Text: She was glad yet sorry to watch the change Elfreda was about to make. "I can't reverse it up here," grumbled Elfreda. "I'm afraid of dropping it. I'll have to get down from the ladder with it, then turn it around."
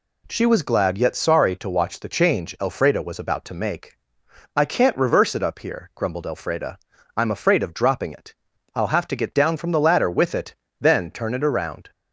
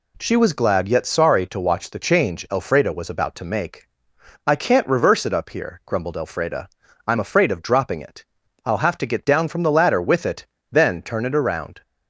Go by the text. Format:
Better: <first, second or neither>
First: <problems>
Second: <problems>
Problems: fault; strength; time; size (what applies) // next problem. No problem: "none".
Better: neither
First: none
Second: none